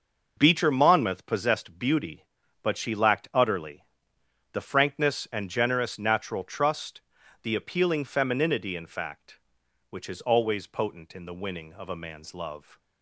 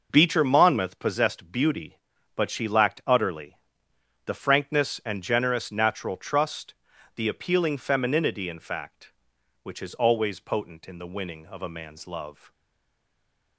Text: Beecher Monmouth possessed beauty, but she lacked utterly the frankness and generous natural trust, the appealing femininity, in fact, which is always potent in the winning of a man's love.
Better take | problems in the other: first | pauses between "utterly" and "the"; noticeable; at 3.5 s; 0.70 s long; noticeable in the first // stays silent after the last word; from 12.5 s on; 1.0 s long

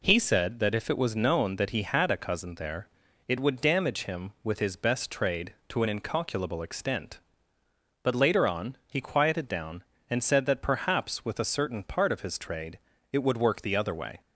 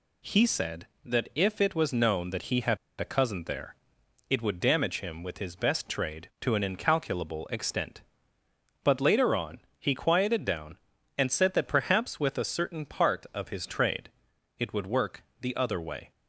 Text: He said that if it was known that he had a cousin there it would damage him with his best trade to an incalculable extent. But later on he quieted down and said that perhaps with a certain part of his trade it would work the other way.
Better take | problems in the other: first | pauses between "had" and "a"; slight; at 2.7 s; 0.23 s long // pauses between "there" and "it"; noticeable; at 3.7 s; 0.54 s long; also in the first // pauses between "on" and "he"; slight; at 9.6 s; 0.18 s long // pauses between "trade" and "it"; noticeable; at 14.1 s; 0.48 s long; slight in the first // pauses between "work" and "the"; slight; at 15.2 s; 0.18 s long

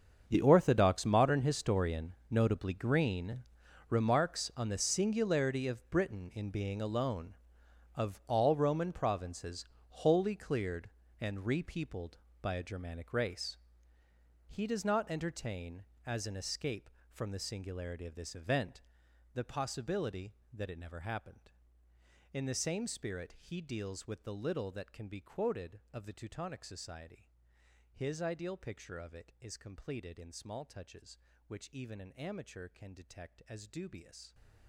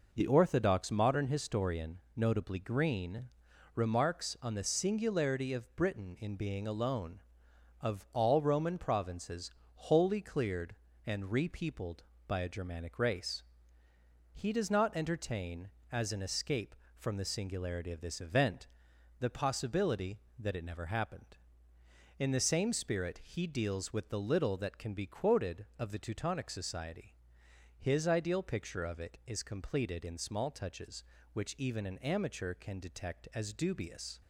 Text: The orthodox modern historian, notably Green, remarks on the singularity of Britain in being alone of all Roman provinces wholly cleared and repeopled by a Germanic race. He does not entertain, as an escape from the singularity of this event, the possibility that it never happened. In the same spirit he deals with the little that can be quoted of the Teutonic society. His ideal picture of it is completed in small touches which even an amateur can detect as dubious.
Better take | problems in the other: second | gets quieter; strong; throughout; 17.5 dB // pauses between "provinces" and "wholly"; slight; at 9.6 s; 0.24 s long; slight in the second

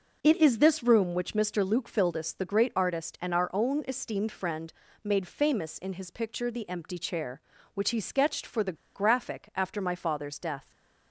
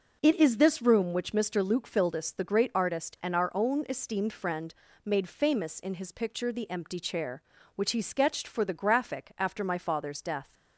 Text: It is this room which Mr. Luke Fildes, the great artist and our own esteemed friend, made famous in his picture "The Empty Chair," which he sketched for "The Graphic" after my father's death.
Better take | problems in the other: second | pauses between "The" and "Graphic"; slight; at 8.7 s; 0.19 s long

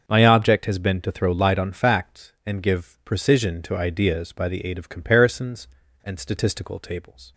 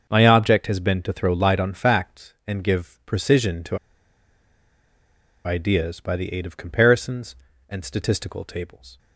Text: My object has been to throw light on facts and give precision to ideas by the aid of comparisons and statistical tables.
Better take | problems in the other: first | starts louder than the rest; until 1.1 s; 6.5 dB; also in the first // pauses between "to" and "ideas"; strong; at 3.7 s; 1.6 s long

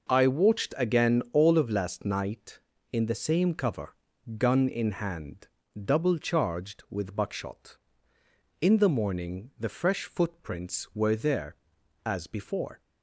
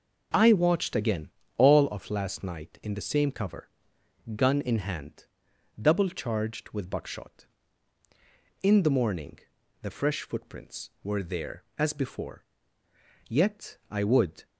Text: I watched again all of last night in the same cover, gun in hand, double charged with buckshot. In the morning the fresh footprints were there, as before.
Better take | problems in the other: first | pauses between "again" and "all"; slight; at 1.2 s; 0.30 s long // pauses between "morning" and "the"; at 9.3 s; 0.42 s long // goes on to say "Yet I would"; noticeable; from 13.2 s on; 1.1 s long

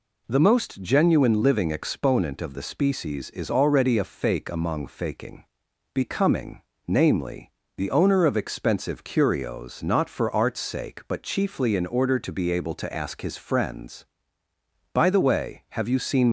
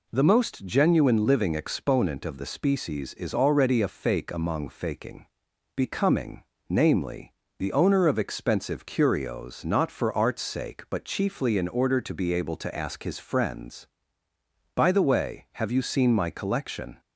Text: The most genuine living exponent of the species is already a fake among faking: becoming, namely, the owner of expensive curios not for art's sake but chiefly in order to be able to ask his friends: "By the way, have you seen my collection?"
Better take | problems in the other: second | stops before "my collection"; at 16.2 s

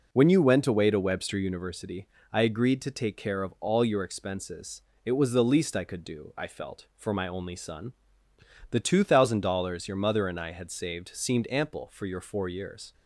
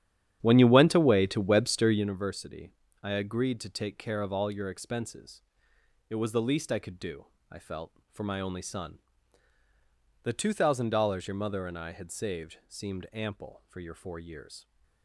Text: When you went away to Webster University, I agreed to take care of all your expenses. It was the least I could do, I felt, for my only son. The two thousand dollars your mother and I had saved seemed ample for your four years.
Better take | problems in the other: first | starts louder than the rest; strong; until 2.1 s; 10 dB

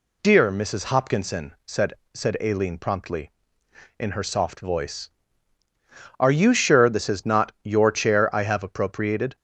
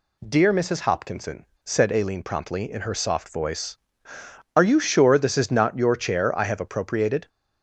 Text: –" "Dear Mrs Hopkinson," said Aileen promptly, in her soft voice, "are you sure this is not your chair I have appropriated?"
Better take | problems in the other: second | says "said" twice; at 2.1 s

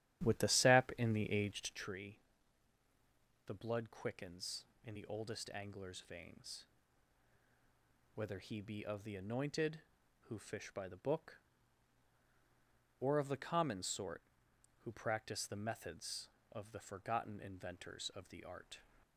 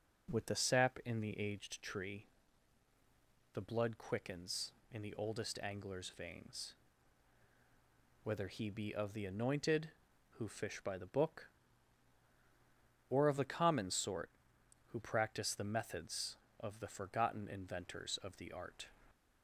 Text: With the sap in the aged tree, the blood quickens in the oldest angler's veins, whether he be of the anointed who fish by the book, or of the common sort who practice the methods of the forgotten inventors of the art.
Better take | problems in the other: second | starts louder than the rest; strong; until 1.9 s; 12.5 dB

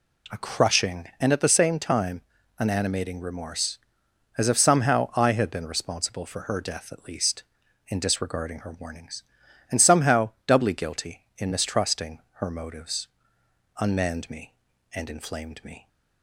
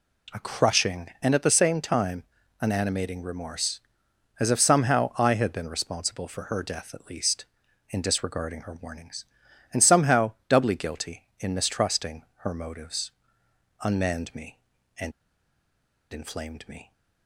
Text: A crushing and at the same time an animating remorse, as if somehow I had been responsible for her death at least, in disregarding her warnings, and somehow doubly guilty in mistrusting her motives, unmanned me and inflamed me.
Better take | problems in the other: first | pauses between "time" and "an"; at 2.2 s; 0.38 s long; also in the first // pauses between "mistrusting" and "her"; slight; at 12.2 s; 0.16 s long; slight in the first // pauses between "and" and "inflamed"; at 15.1 s; 1.0 s long

